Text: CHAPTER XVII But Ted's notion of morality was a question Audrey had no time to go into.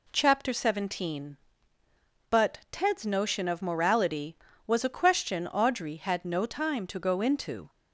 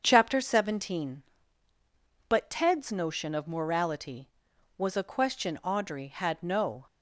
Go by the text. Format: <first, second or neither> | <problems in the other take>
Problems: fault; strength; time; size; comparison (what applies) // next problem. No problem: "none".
first | starts louder than the rest; until 1.0 s; 7 dB // stops before "time to go into"; at 6.8 s